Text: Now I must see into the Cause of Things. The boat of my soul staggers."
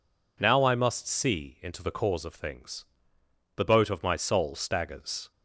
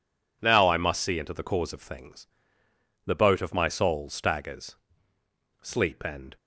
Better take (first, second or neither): first